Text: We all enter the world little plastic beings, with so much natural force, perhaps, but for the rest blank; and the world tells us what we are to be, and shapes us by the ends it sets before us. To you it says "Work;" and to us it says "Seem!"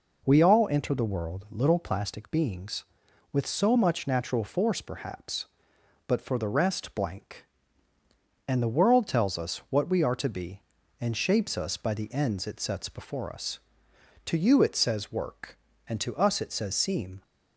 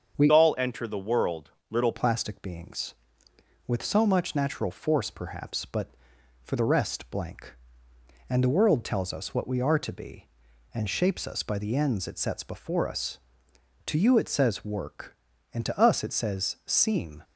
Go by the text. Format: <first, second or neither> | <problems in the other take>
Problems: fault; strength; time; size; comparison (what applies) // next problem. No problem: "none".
first | starts louder than the rest; until 1.2 s; 7 dB // changes voice from "all" to "little"; from 0.3 to 1.9 s; 1.6 s long // pauses between "world" and "little"; slight; at 1.5 s; 0.18 s long